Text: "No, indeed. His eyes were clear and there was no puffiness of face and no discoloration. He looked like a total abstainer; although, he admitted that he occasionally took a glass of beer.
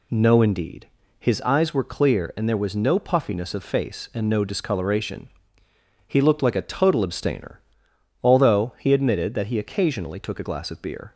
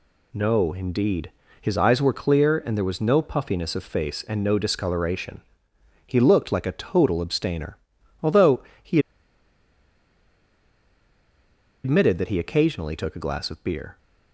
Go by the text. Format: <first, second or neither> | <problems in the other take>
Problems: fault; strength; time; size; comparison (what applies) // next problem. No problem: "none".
first | pauses between "he" and "admitted"; strong; at 8.9 s; 2.8 s long